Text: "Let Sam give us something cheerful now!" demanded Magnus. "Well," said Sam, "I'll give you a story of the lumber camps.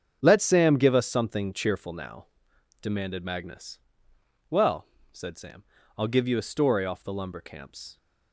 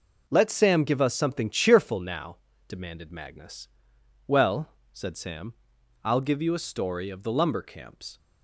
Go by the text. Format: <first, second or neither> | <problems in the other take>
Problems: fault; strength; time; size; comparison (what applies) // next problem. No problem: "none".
second | starts louder than the rest; strong; until 1.2 s; 7.5 dB // says "off" for "of"; at 6.8 s